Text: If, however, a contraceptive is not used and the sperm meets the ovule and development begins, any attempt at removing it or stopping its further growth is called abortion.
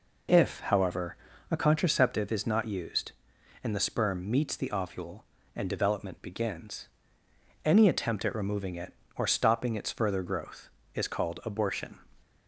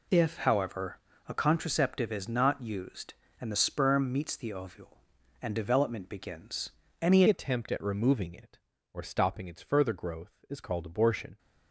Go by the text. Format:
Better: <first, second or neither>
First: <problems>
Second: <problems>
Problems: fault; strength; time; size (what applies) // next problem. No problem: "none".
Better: first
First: none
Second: changes voice at "attempt"; from 7.2 s on; 4.1 s long